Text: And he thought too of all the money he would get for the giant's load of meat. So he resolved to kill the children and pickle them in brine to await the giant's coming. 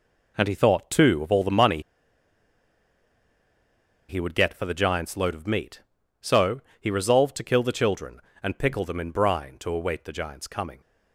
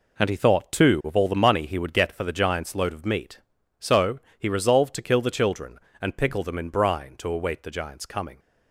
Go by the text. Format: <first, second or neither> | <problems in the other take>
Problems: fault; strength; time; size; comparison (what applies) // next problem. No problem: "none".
second | pauses between "money" and "he"; strong; at 1.8 s; 2.2 s long // pauses between "So" and "he"; slight; at 6.6 s; 0.18 s long; slight in the second